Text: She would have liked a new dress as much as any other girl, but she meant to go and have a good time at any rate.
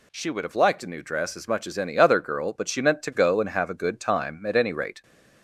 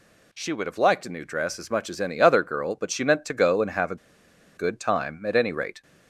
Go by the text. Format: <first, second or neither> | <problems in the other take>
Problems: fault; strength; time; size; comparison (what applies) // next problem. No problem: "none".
first | pauses between "a" and "good"; noticeable; at 3.9 s; 0.61 s long